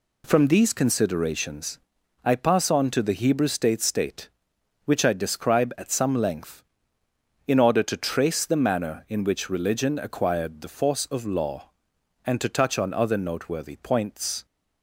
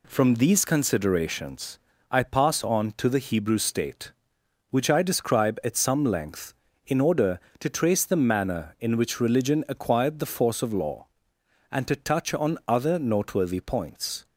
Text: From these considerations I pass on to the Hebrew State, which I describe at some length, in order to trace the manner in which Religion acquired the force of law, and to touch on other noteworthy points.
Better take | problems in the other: second | pauses between "considerations" and "I"; noticeable; at 1.7 s; 0.46 s long; slight in the second // says "State" twice; at 3.7 s

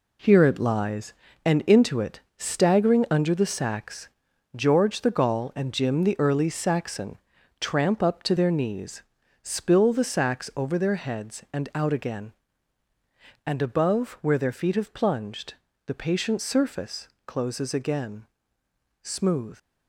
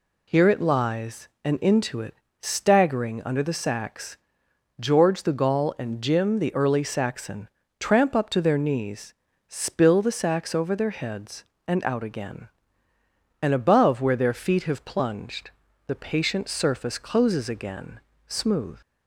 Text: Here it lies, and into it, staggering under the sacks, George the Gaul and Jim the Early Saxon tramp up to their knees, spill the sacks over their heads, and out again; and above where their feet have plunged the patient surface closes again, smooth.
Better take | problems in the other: second | gets quieter; strong; throughout; 8.5 dB // pauses between "Saxon" and "tramp"; at 7.1 s; 0.42 s long; slight in the second // pauses between "plunged" and "the"; slight; at 15.5 s; 0.32 s long; slight in the second // pauses between "surface" and "closes"; slight; at 17.0 s; 0.18 s long

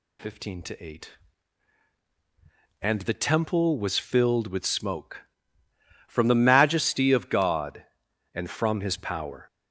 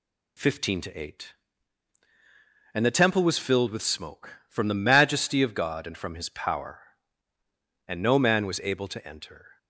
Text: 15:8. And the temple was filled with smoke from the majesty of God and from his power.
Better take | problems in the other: first | goes on to say "And no man was able to enter"; strong; from 7.8 s on; 1.7 s long

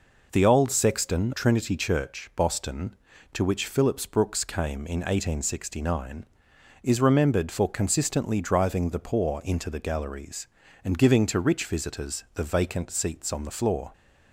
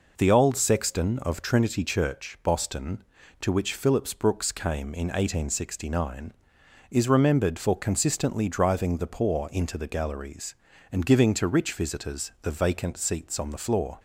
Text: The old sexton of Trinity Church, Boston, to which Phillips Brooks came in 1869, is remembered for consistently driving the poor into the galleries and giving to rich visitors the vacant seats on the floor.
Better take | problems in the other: second | skips "of"; at 1.3 s

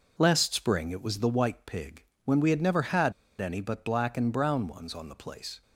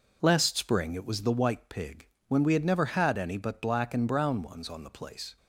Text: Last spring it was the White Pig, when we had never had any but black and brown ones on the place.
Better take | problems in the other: second | pauses between "had" and "any"; slight; at 3.1 s; 0.26 s long

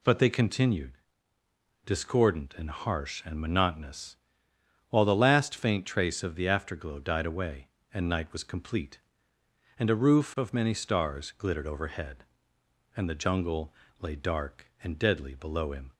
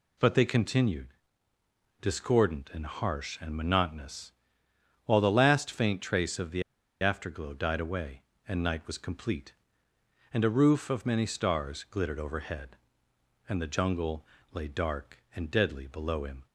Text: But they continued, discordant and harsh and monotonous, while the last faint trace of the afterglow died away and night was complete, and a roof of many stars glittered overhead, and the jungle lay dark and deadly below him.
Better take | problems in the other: first | pauses between "the" and "afterglow"; at 6.6 s; 0.39 s long // pauses between "jungle" and "lay"; slight; at 14.2 s; 0.28 s long; slight in the first

